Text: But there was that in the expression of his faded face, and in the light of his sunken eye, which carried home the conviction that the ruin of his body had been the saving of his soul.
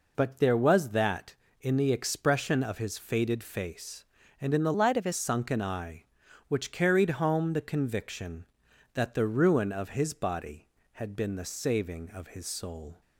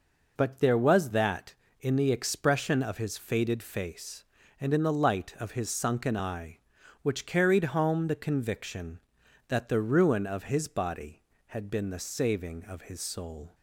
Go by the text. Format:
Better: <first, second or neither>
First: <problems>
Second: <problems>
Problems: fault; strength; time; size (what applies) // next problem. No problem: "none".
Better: second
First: changes voice from "light" to "his"; from 4.7 to 5.1 s; 0.4 s long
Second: none